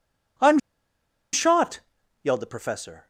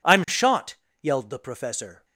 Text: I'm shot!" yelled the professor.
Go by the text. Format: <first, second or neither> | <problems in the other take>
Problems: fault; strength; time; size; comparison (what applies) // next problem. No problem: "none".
second | pauses between "I'm" and "shot"; noticeable; at 0.5 s; 0.74 s long